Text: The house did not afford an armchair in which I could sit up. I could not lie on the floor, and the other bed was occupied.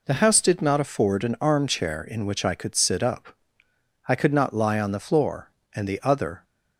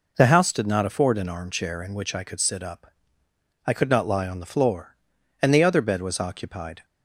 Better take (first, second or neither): second